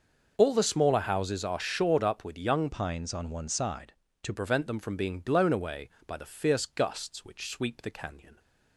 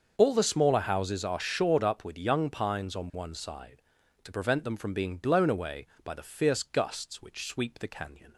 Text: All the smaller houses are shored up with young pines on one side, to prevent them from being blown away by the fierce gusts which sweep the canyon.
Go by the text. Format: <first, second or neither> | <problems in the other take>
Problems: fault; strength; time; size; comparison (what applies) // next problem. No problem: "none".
second | starts louder than the rest; until 1.3 s; 6 dB; also in the second // changes voice from "pines" to "to"; from 2.7 to 4.3 s; 1.6 s long